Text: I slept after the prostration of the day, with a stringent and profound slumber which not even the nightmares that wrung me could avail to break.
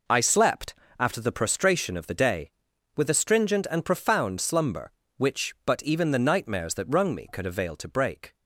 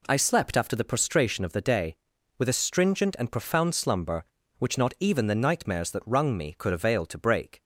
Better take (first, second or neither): second